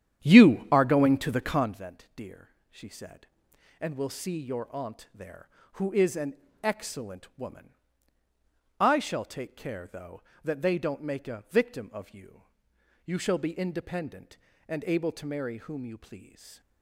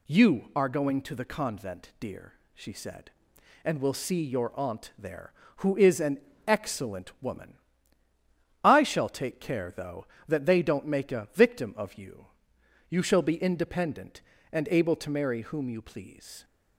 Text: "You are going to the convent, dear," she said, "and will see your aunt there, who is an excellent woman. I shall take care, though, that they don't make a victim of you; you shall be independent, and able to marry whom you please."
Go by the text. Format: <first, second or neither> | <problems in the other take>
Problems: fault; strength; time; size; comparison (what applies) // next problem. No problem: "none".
second | starts louder than the rest; strong; until 1.9 s; 10 dB // pauses between "an" and "excellent"; slight; at 6.3 s; 0.26 s long; slight in the second